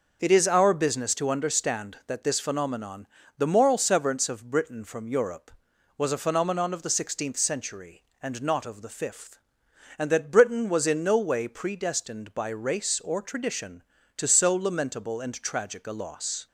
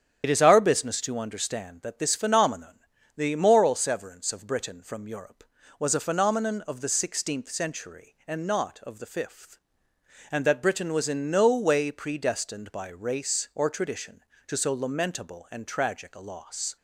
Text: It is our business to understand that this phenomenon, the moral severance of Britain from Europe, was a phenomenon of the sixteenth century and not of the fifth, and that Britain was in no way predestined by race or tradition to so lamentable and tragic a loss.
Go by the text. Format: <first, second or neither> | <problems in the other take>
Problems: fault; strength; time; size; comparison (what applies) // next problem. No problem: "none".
first | loses the start of "It"; at 0.2 s; 40 ms // starts louder than the rest; strong; until 1.2 s; 9 dB